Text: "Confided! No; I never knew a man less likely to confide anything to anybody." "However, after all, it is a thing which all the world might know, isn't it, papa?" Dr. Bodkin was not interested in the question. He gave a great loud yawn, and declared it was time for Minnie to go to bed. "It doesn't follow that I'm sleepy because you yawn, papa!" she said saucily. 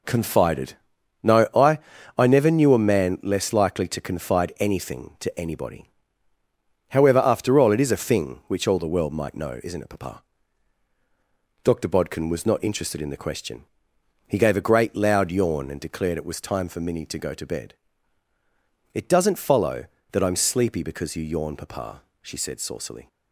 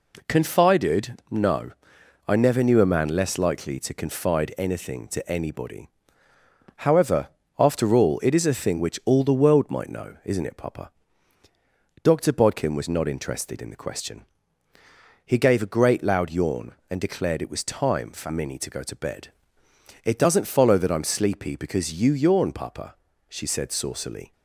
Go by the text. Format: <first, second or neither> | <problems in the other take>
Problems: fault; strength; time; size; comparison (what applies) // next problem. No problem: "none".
second | says "I" twice; at 2.1 s